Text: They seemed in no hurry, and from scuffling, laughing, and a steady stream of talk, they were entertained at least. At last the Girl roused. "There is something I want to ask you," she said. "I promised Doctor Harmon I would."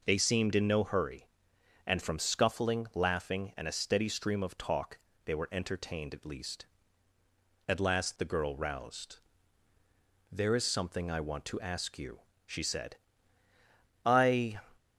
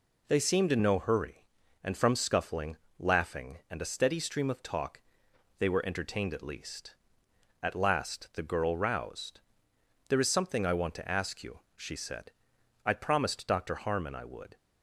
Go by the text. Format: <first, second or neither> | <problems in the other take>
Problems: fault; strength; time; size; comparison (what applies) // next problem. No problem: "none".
second | stops before "promised Doctor Harmon I would"; at 14.7 s